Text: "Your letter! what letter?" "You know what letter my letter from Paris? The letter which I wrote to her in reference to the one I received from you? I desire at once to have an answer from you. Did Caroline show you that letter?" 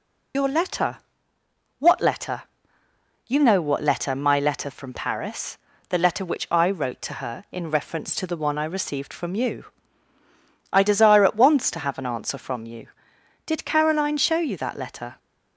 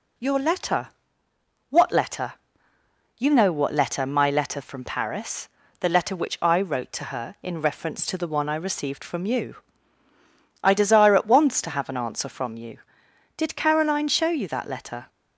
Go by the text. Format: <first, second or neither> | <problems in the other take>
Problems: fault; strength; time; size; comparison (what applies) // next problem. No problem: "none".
second | loses the start of "Your"; at 0.3 s; 75 ms